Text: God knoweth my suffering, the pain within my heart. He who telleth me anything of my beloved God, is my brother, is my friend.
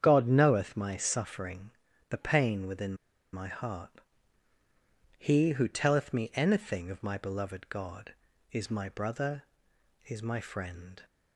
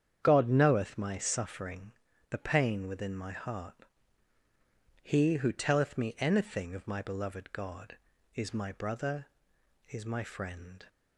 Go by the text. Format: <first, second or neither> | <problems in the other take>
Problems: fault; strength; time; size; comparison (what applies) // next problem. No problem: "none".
second | starts louder than the rest; strong; until 1.0 s; 8.5 dB; strong in the second // pauses between "within" and "my"; at 2.9 s; 0.38 s long